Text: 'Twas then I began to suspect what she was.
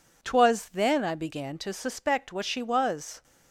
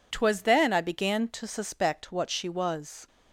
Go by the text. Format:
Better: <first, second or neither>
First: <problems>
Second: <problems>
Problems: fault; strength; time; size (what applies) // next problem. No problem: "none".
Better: neither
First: none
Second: none